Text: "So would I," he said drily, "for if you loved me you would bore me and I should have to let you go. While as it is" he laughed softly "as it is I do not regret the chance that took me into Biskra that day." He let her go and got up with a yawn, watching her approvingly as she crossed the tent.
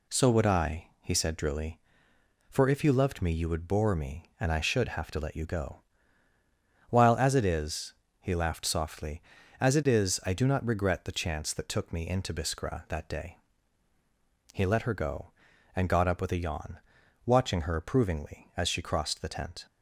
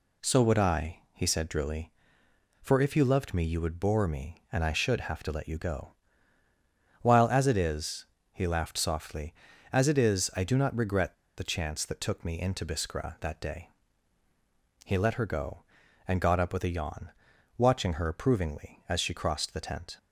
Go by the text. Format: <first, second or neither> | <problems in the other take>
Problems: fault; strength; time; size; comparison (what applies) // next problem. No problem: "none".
first | pauses between "is" and "he"; slight; at 8.0 s; 0.26 s long; slight in the first // pauses between "regret" and "the"; slight; at 11.1 s; 0.23 s long